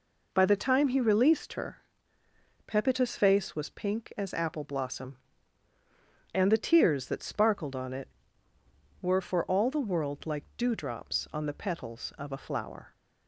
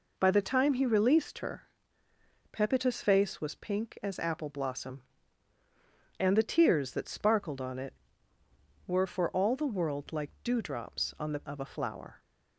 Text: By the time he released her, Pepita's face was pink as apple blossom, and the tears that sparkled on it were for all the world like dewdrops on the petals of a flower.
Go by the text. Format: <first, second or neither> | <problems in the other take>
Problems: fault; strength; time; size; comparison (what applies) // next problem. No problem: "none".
first | skips "petals"; at 11.4 s